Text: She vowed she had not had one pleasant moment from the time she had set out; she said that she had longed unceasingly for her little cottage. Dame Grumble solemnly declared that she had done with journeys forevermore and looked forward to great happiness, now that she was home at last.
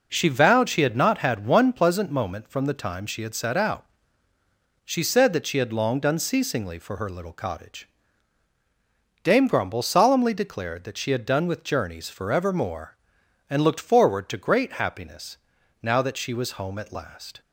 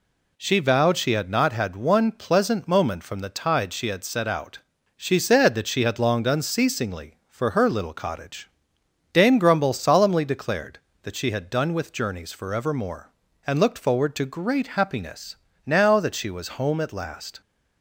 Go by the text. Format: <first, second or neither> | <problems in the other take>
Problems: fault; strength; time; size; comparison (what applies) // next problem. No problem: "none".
first | says "tide" for "time"; at 3.2 s